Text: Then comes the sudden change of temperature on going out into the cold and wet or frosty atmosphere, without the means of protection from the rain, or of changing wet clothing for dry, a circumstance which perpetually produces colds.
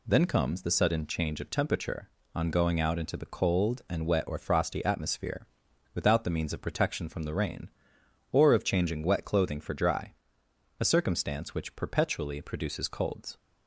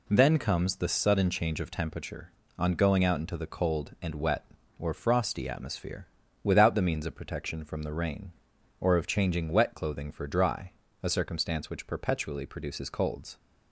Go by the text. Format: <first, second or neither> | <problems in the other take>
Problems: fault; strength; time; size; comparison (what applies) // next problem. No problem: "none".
neither | none